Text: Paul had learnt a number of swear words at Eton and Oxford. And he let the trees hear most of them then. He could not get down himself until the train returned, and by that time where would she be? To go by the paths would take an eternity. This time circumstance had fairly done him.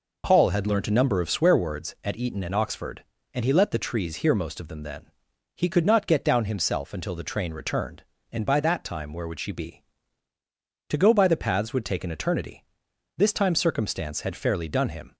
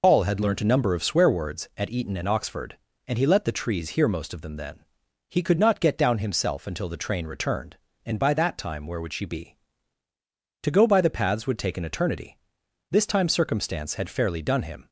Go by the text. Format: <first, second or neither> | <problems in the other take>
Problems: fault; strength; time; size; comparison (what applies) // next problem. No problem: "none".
first | loses the start of "Paul"; at 0.0 s; 60 ms